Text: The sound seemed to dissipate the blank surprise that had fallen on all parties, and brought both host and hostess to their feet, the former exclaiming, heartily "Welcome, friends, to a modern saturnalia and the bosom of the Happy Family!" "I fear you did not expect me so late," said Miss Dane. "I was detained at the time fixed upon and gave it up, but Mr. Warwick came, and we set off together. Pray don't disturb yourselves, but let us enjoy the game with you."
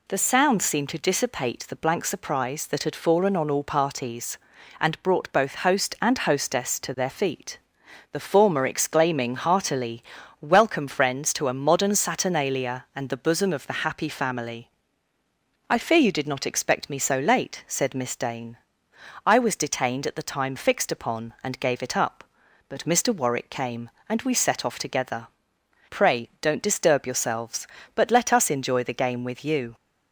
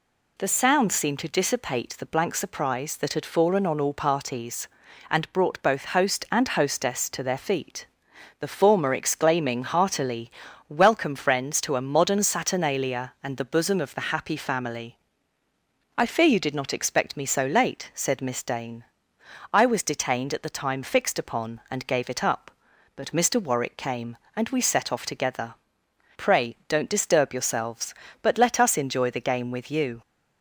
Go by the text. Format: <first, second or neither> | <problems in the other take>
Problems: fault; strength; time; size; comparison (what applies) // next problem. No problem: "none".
neither | pauses between "heartily" and "Welcome"; slight; the same in both